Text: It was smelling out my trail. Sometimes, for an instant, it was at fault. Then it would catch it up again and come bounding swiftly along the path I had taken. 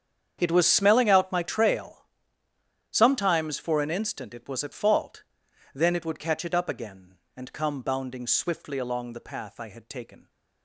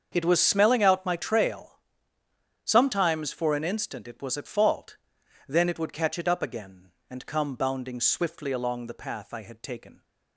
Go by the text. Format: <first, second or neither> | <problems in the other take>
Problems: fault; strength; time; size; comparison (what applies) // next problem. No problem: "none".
second | gets quieter; strong; throughout; 16.5 dB // starts louder than the rest; strong; until 1.4 s; 8 dB; also in the second